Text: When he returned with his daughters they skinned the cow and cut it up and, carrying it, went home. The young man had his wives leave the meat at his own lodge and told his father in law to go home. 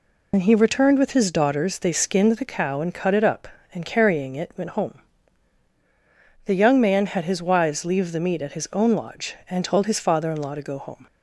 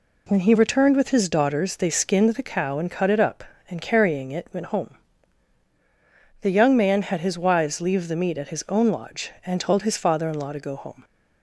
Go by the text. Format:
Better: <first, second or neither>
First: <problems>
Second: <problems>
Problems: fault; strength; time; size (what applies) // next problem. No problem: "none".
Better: second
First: loses the start of "When"; at 0.3 s; 65 ms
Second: none